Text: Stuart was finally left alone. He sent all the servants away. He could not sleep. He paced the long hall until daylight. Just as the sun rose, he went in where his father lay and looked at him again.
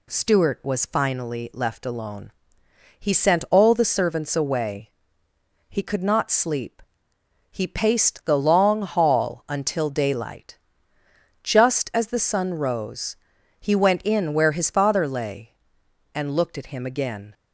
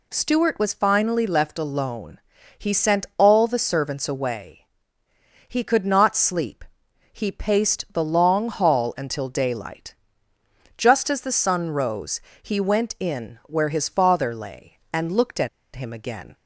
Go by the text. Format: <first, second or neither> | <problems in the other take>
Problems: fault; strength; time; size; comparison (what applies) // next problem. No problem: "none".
first | pauses between "at" and "him"; slight; at 15.4 s; 0.26 s long